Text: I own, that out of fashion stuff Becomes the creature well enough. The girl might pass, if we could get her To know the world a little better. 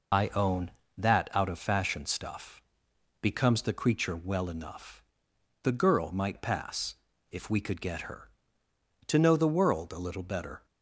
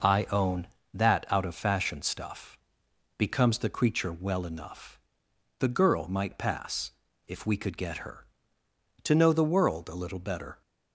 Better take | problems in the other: second | loses the start of "I"; at 0.1 s; 80 ms // pauses between "stuff" and "Becomes"; noticeable; at 2.6 s; 0.60 s long; noticeable in the second

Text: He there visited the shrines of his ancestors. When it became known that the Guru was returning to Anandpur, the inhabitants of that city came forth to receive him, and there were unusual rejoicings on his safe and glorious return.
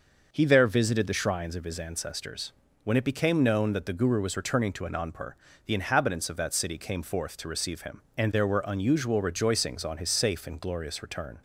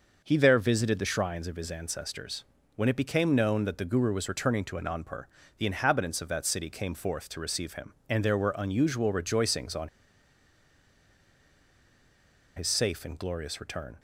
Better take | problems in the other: first | pauses between "on" and "his"; strong; at 9.8 s; 2.6 s long

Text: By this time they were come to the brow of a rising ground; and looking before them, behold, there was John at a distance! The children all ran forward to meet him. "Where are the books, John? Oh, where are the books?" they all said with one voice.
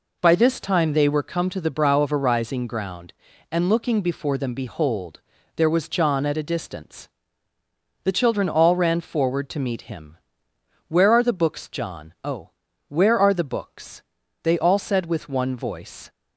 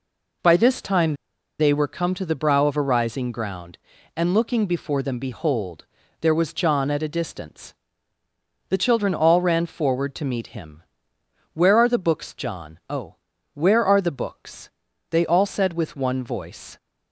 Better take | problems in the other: first | pauses between "time" and "they"; at 1.1 s; 0.44 s long

